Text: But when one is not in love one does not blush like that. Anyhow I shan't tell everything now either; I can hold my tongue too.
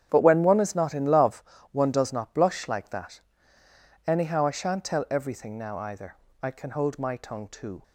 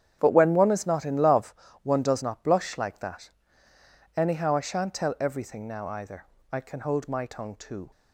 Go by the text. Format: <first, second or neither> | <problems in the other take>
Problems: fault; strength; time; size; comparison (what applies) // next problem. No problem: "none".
neither | starts louder than the rest; strong; the same in both // pauses between "love" and "one"; slight; the same in both